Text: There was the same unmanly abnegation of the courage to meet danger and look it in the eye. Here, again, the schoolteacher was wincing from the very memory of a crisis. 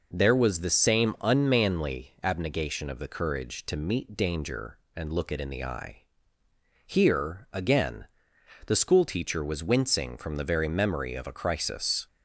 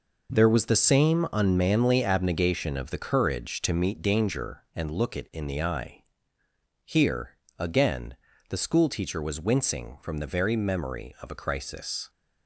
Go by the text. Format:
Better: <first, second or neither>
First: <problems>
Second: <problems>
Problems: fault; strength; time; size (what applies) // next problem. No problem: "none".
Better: first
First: none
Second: gets quieter; strong; throughout; 9 dB